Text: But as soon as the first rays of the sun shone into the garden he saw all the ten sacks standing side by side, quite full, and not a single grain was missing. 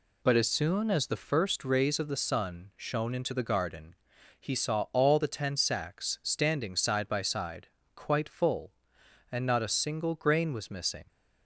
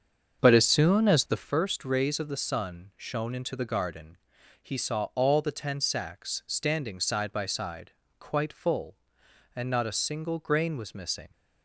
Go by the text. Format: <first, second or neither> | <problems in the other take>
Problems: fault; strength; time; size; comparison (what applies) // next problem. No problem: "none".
first | starts louder than the rest; until 1.5 s; 7 dB // pauses between "garden" and "he"; noticeable; at 4.1 s; 0.48 s long; noticeable in the first